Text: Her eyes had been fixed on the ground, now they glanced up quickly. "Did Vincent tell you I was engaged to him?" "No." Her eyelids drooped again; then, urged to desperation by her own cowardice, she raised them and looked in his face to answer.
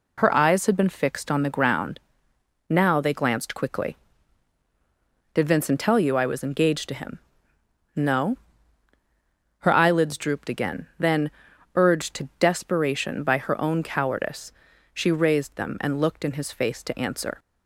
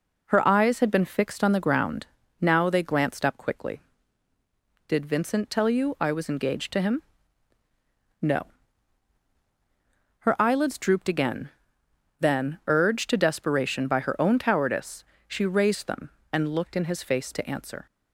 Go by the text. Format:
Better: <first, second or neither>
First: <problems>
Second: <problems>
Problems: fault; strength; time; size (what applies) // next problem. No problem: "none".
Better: second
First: skips "up"; at 3.5 s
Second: none